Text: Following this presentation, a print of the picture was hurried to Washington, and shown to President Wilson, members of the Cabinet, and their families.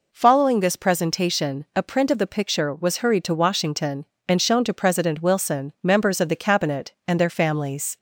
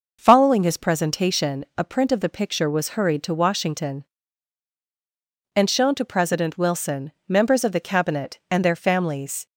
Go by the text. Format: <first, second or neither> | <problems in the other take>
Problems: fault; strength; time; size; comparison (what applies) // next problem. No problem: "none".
first | says "his" for "this"; at 0.6 s